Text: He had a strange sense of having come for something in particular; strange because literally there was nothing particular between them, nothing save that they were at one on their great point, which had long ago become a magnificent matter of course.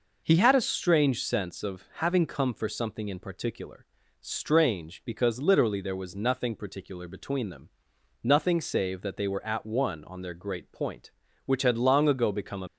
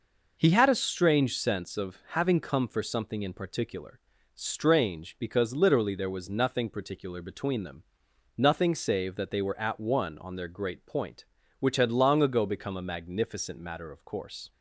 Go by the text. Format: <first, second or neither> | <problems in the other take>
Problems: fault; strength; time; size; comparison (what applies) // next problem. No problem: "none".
second | stops before "magnificent matter of course"; at 12.6 s